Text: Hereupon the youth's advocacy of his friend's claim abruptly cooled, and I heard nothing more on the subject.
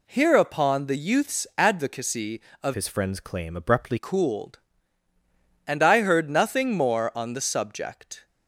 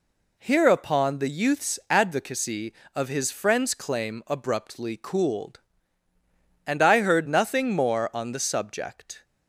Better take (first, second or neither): second